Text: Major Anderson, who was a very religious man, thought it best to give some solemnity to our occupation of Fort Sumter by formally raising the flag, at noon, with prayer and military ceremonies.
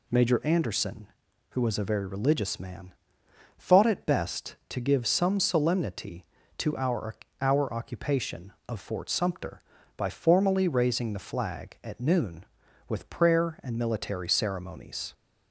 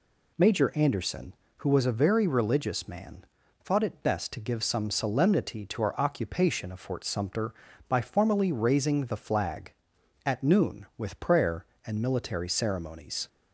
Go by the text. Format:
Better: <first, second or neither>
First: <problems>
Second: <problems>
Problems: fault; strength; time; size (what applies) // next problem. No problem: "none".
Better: second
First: says "our" twice; at 7.4 s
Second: none